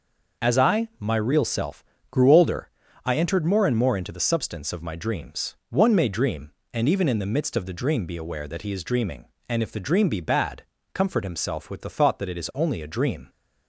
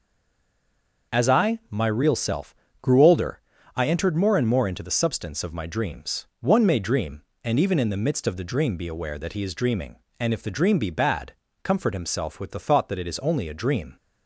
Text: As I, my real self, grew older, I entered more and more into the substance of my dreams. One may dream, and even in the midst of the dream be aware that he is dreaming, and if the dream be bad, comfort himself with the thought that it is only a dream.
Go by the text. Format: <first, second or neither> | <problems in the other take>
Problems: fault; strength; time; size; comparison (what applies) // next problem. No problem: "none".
first | stays silent before the first word; until 1.1 s; 1.1 s long